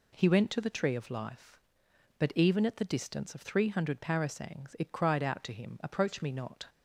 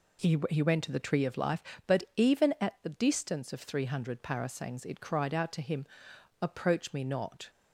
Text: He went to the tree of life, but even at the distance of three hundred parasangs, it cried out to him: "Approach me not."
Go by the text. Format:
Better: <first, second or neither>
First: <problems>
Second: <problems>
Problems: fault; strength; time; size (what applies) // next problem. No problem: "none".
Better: first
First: none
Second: says "He" twice; at 0.4 s